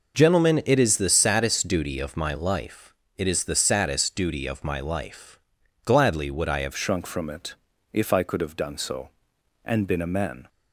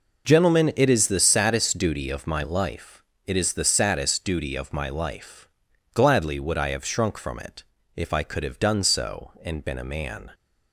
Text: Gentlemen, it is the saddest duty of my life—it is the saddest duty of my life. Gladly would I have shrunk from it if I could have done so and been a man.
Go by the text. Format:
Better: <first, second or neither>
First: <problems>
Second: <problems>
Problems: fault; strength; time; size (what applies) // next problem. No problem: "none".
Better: second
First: changes voice at "shrunk"; from 6.7 s on; 3.7 s long // pauses between "it" and "if"; at 7.5 s; 0.38 s long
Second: pauses between "it" and "if"; slight; at 7.6 s; 0.32 s long